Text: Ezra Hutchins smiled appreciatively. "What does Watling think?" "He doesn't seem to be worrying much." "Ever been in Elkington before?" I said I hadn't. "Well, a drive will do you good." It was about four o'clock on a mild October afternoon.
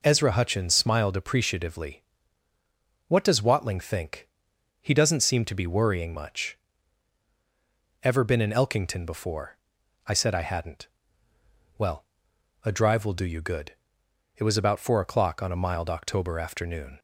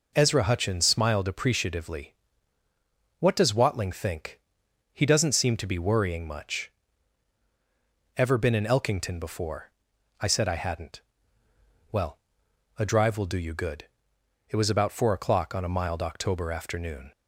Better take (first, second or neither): neither